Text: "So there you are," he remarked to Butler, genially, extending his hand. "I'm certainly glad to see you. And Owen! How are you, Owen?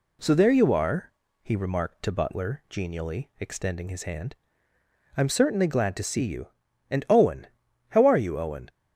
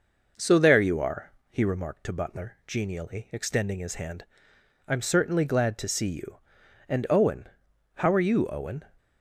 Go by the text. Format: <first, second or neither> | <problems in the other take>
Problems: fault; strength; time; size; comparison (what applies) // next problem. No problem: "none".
first | starts louder than the rest; noticeable; until 1.4 s; 5.5 dB